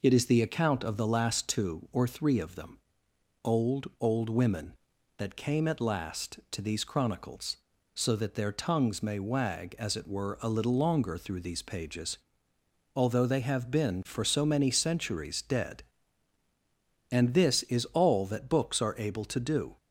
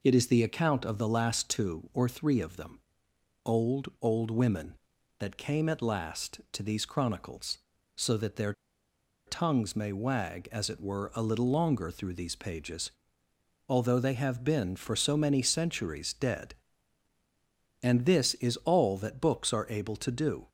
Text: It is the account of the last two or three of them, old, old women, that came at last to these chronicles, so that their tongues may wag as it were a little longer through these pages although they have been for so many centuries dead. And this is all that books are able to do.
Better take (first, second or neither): first